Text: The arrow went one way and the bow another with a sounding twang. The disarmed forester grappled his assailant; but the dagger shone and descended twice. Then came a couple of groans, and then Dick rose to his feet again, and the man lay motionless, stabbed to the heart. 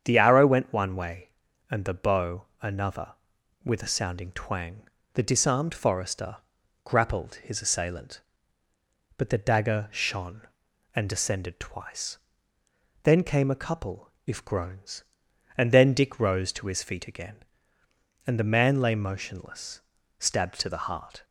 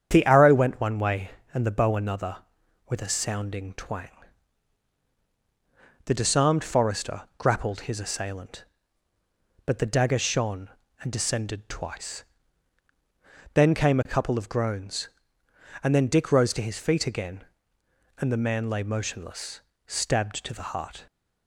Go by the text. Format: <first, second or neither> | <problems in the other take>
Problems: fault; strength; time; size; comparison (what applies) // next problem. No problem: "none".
second | starts louder than the rest; strong; until 1.0 s; 8 dB; strong in the second // pauses between "bow" and "another"; slight; at 2.4 s; 0.16 s long // pauses between "forester" and "grappled"; noticeable; at 6.3 s; 0.48 s long; slight in the second // says "if" for "of"; at 14.2 s